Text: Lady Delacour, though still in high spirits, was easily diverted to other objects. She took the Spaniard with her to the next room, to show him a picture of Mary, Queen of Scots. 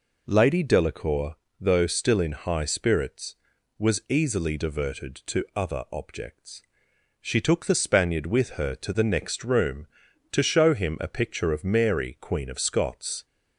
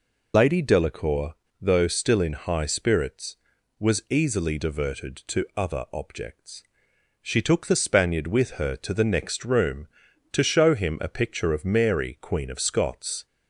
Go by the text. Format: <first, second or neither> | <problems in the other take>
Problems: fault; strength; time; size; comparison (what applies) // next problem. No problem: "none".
first | loses the start of "Lady"; at 0.3 s; 85 ms